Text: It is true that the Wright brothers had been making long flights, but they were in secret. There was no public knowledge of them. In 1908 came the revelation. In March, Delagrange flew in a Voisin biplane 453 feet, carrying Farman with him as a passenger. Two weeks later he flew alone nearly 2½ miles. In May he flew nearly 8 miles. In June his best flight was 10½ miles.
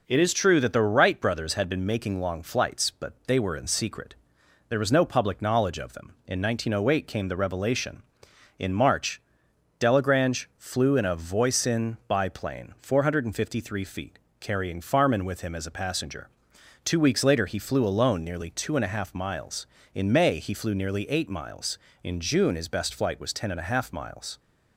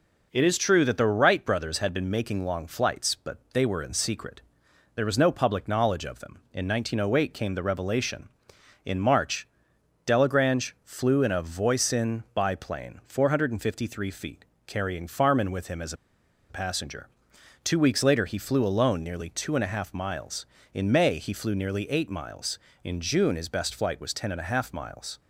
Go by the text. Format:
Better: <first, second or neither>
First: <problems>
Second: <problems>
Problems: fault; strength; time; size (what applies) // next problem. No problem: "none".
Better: first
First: none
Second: pauses between "as" and "a"; noticeable; at 15.9 s; 0.56 s long